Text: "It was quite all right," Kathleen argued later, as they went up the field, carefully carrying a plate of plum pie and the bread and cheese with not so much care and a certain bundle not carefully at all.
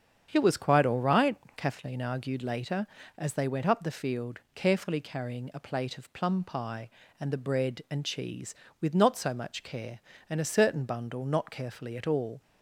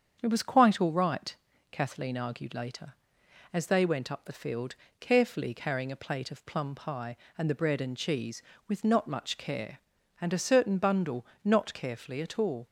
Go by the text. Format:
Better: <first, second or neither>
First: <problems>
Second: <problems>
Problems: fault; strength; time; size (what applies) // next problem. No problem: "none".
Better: first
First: starts louder than the rest; strong; until 1.3 s; 8 dB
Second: starts louder than the rest; strong; until 1.2 s; 7.5 dB // skips "so"; at 9.0 s // pauses between "bundle" and "not"; slight; at 11.2 s; 0.18 s long